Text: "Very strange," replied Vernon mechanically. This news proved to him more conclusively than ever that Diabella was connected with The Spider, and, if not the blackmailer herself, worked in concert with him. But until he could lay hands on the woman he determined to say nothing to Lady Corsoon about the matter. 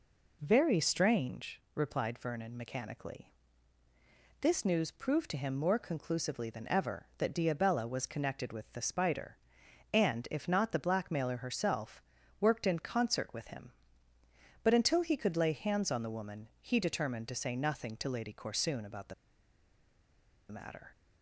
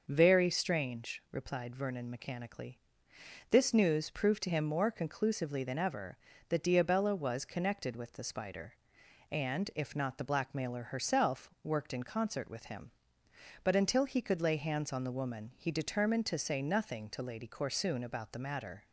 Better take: second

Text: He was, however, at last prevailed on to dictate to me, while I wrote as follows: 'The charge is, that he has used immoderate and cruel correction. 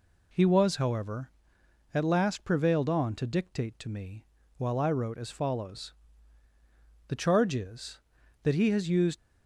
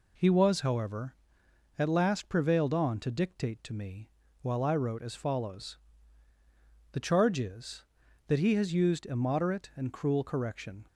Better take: second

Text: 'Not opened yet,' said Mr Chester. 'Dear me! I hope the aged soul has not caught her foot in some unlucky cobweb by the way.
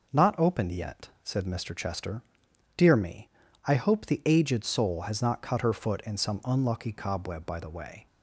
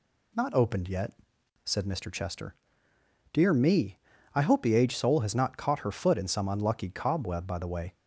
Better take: second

